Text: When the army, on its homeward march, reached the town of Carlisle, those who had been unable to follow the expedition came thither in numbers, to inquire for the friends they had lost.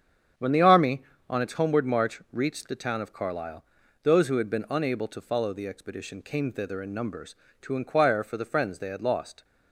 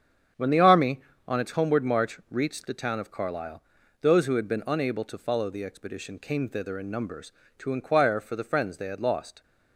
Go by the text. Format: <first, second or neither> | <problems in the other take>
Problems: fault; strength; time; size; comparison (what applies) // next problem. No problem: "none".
neither | starts louder than the rest; strong; the same in both